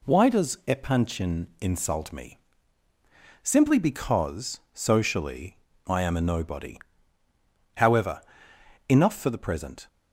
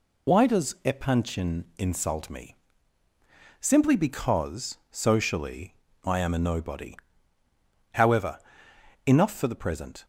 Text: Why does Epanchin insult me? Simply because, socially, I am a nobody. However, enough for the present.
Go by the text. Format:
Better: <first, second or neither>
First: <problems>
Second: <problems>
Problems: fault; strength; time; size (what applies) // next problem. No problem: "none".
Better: first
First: none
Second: loses the start of "Why"; at 0.2 s; 75 ms